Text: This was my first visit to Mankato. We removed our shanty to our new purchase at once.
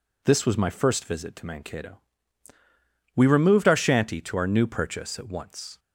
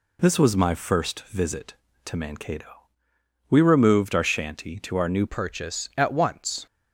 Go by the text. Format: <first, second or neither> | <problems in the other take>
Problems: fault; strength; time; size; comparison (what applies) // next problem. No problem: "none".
first | changes voice at "purchase"; from 5.2 s on; 1.4 s long